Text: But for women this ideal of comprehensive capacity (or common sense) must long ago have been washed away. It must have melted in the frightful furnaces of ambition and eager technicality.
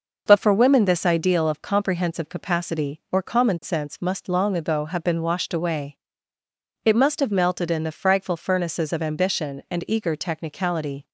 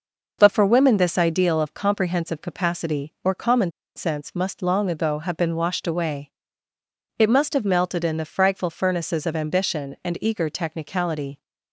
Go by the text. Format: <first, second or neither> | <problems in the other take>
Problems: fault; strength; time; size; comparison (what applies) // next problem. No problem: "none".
first | pauses between "common" and "sense"; slight; at 3.7 s; 0.24 s long